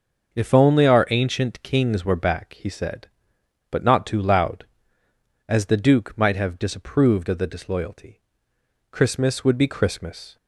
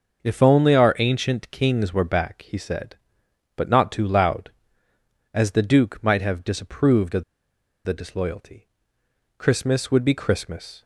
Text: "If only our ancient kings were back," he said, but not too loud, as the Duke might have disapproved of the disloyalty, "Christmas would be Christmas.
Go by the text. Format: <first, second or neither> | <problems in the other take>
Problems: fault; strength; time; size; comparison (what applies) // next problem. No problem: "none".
first | starts louder than the rest; until 1.2 s; 6.5 dB; also in the first // pauses between "of" and "the"; noticeable; at 7.2 s; 0.61 s long